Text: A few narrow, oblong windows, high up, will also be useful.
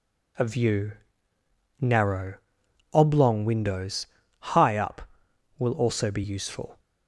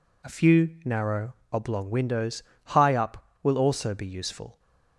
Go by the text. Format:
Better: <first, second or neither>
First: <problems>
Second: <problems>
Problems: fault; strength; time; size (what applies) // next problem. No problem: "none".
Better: second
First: says "view" for "few"; at 0.4 s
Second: none